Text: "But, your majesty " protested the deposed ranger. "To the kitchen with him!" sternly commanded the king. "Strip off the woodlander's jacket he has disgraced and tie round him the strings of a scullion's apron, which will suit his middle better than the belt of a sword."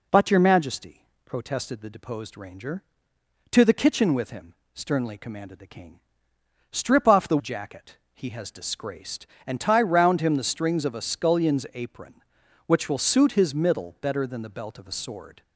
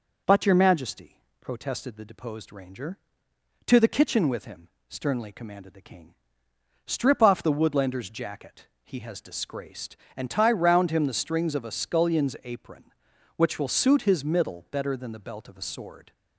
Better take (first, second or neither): second